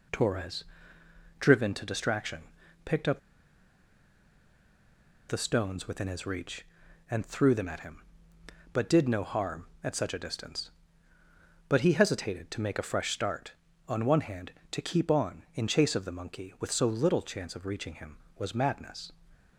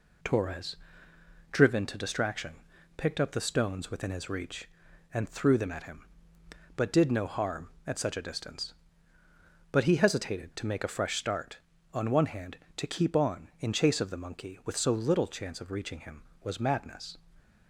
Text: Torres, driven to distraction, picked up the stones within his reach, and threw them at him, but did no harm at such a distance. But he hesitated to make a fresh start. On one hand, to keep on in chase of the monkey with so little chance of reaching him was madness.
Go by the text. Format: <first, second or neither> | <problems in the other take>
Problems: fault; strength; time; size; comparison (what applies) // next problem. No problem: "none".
second | pauses between "up" and "the"; strong; at 3.1 s; 2.0 s long